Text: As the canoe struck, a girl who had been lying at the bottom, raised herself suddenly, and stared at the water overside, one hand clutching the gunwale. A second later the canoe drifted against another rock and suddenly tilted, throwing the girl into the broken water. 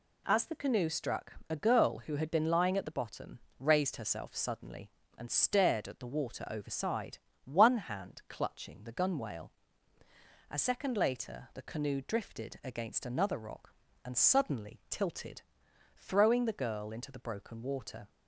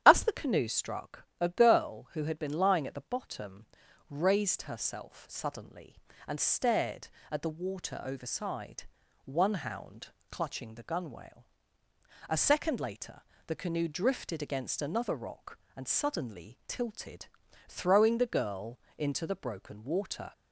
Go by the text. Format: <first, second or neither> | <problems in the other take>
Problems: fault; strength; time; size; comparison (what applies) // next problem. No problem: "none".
first | starts louder than the rest; strong; until 1.0 s; 10 dB // says "hound" for "hand"; at 9.5 s // pauses between "later" and "the"; slight; at 13.2 s; 0.24 s long // pauses between "girl" and "into"; slight; at 18.8 s; 0.18 s long